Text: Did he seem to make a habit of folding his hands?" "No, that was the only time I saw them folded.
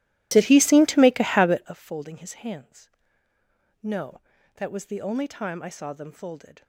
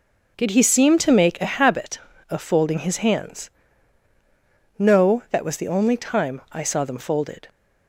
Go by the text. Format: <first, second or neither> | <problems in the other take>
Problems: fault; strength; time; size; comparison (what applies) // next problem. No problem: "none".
second | starts louder than the rest; strong; until 1.8 s; 15 dB